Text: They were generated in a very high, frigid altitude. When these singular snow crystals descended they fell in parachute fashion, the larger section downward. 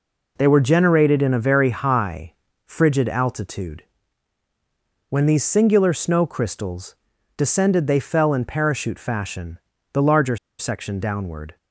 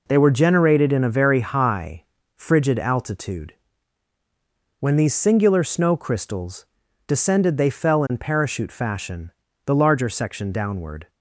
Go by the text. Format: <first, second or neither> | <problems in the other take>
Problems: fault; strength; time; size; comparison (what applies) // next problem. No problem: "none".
second | pauses between "crystals" and "descended"; at 6.9 s; 0.42 s long; also in the second // pauses between "larger" and "section"; slight; at 10.3 s; 0.22 s long